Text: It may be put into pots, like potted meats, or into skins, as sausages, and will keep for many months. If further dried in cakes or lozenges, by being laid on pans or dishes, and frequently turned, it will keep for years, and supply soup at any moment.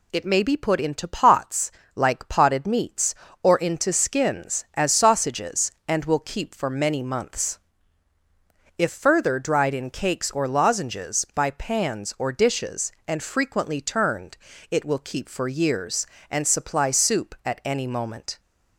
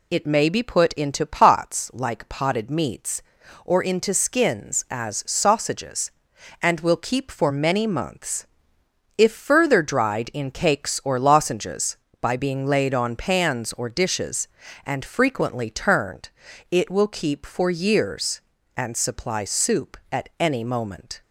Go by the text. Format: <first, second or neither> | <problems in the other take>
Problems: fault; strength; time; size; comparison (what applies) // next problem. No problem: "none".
second | skips "being laid on"; at 11.5 s